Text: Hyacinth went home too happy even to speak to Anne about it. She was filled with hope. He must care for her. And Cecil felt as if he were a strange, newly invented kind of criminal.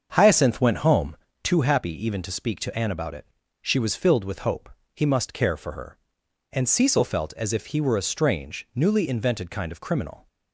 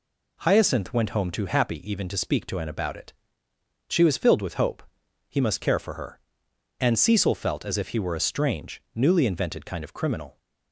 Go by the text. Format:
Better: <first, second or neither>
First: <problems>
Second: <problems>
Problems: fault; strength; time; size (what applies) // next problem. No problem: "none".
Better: second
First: starts louder than the rest; until 1.3 s; 7 dB // pauses between "home" and "too"; slight; at 1.1 s; 0.26 s long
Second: none